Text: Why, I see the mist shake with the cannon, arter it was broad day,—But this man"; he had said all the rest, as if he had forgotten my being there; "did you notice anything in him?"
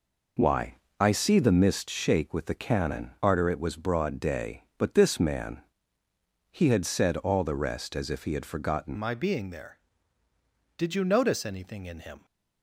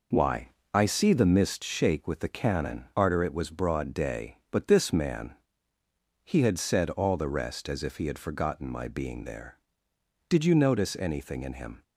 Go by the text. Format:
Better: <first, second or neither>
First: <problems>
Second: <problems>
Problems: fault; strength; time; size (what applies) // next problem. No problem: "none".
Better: second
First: changes voice at "my"; from 8.9 s on; 3.3 s long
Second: none